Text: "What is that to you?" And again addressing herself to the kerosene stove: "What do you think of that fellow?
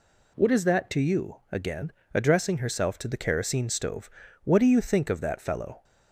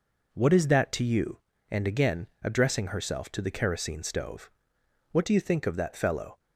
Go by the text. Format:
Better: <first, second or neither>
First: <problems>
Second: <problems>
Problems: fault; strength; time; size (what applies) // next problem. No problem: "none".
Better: second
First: skips "And"; at 1.4 s // pauses between "again" and "addressing"; slight; at 1.9 s; 0.20 s long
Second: none